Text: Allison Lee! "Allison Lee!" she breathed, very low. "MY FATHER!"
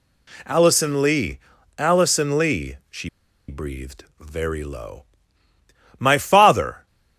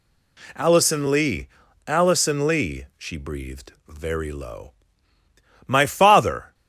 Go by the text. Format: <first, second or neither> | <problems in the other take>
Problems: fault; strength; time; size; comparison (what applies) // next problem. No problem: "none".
second | pauses between "she" and "breathed"; at 3.0 s; 0.40 s long